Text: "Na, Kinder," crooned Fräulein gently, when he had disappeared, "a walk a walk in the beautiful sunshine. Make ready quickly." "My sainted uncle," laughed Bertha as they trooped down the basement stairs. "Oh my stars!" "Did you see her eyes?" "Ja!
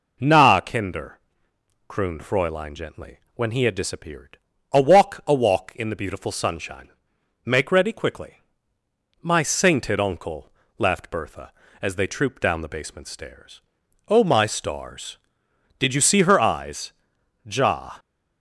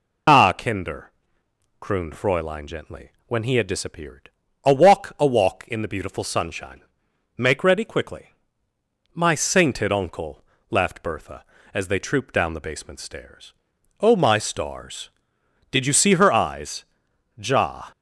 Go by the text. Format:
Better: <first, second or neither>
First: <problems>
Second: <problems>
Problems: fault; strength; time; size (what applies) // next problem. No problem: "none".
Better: first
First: none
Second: loses the start of "Na"; at 0.2 s; 155 ms